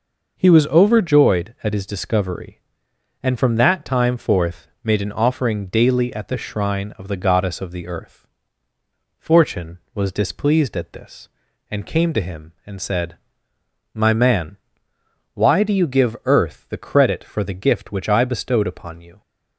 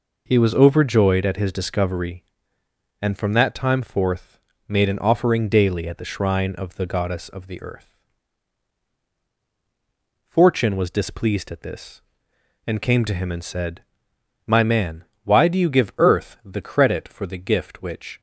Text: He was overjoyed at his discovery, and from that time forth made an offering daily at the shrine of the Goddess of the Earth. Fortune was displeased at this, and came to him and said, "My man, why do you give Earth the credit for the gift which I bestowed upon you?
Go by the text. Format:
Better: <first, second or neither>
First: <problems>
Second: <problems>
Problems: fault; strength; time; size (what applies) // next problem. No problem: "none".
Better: first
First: pauses between "forth" and "made"; slight; at 4.6 s; 0.16 s long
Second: pauses between "forth" and "made"; slight; at 4.4 s; 0.26 s long // stops before "I bestowed upon you"; at 18.1 s